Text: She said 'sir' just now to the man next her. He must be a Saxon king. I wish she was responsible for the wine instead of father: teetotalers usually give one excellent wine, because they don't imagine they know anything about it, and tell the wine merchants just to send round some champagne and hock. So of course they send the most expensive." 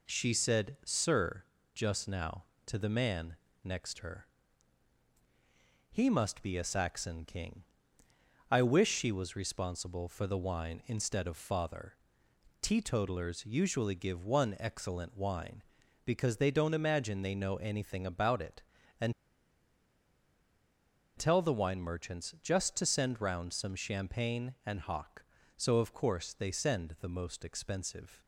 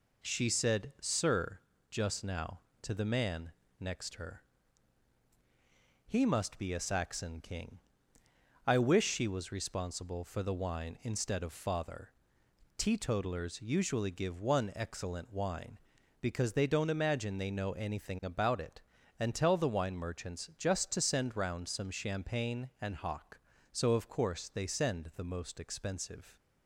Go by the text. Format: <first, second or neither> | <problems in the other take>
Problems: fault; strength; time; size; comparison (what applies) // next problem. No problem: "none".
second | pauses between "sir" and "just"; slight; at 1.4 s; 0.30 s long; slight in the second // pauses between "man" and "next"; slight; at 3.3 s; 0.28 s long; slight in the second // pauses between "and" and "tell"; strong; at 19.1 s; 2.0 s long